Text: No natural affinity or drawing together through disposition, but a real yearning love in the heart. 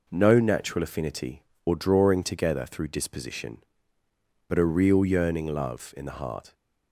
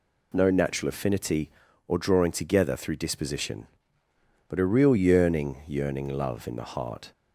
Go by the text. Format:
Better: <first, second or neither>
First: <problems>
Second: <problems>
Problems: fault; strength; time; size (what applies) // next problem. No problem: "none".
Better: first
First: none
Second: says "yearning" twice; at 5.6 s